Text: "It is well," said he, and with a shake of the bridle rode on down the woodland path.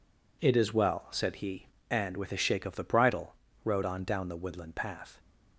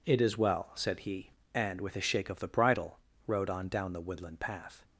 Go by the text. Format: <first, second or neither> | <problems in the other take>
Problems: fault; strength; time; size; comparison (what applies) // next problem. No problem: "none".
neither | pauses between "bridle" and "rode"; slight; the same in both